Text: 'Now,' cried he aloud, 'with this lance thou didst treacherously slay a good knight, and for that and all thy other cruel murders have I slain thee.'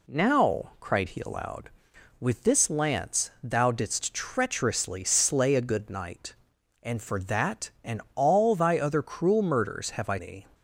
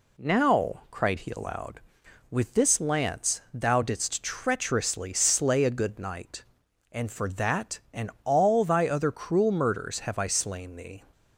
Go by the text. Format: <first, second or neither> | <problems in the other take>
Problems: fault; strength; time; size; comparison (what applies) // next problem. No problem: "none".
second | skips "slain"; at 10.1 s